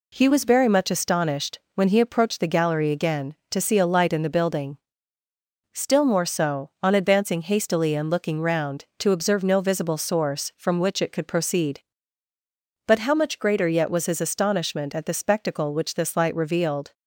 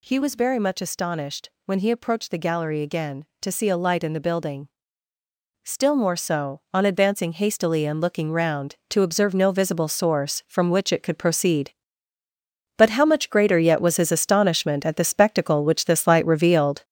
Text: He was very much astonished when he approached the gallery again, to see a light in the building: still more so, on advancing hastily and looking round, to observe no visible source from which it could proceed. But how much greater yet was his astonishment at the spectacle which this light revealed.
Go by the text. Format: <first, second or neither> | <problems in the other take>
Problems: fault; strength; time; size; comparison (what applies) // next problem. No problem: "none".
first | gets louder; noticeable; throughout; 6 dB // pauses between "astonished" and "when"; slight; at 1.4 s; 0.16 s long; slight in the first